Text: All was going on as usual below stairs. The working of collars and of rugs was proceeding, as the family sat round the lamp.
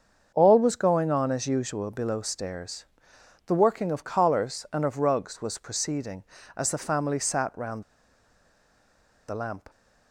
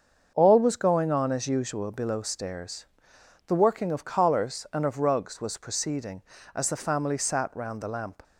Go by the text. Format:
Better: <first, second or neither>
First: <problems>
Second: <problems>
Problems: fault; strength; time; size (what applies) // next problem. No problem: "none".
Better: second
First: starts louder than the rest; until 1.3 s; 7 dB // pauses between "round" and "the"; strong; at 7.8 s; 1.4 s long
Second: starts louder than the rest; until 1.3 s; 6.5 dB